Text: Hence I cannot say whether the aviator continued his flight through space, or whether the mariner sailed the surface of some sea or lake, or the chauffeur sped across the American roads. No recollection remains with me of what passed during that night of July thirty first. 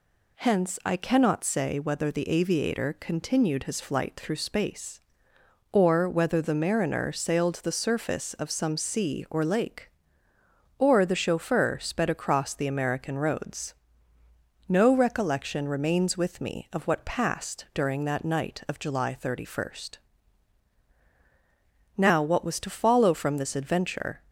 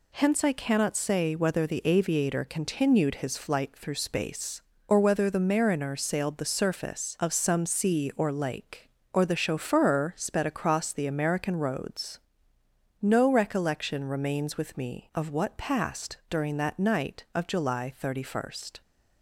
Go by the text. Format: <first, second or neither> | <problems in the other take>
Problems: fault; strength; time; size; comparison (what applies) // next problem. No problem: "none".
second | goes on to say "Now what was to follow from this adventure"; strong; from 21.9 s on; 2.2 s long